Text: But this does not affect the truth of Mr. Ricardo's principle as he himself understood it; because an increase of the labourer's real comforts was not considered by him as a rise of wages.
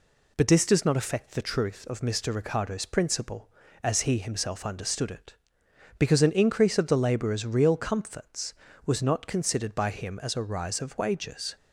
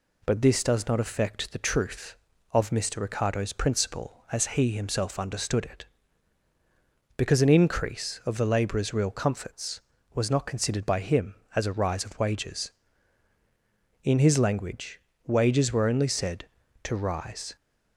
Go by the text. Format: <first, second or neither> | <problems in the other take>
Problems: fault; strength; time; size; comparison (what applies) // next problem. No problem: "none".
first | goes on to say "In his language wages were only said to rise"; strong; from 14.0 s on; 3.5 s long